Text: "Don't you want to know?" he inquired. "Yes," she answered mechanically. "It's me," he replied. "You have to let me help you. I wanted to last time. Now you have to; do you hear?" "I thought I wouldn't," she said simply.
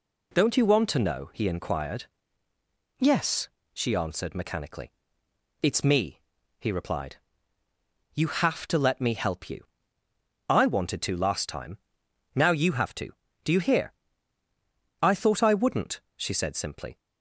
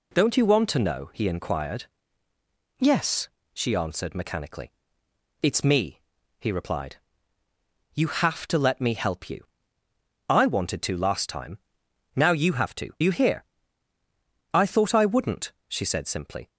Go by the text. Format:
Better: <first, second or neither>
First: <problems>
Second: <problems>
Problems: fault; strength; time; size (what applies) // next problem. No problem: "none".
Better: first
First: none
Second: skips "do"; at 12.9 s